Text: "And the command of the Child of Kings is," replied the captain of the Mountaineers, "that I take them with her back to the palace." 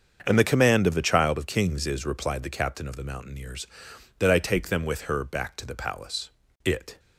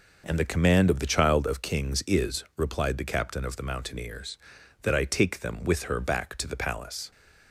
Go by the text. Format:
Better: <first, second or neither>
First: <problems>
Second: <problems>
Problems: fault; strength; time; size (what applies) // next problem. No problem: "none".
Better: second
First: starts louder than the rest; until 1.2 s; 7 dB // goes on to say "It"; slight; from 6.6 s on; 0.36 s long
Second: none